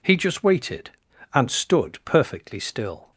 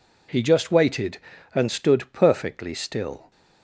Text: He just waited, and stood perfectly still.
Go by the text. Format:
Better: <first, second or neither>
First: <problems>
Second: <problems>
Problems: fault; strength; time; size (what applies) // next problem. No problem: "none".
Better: neither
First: none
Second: none